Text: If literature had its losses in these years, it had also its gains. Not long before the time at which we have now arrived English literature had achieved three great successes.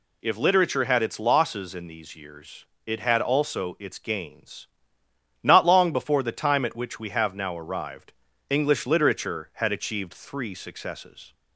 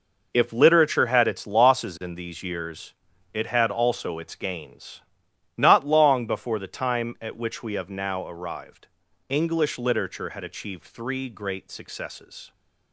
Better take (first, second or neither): second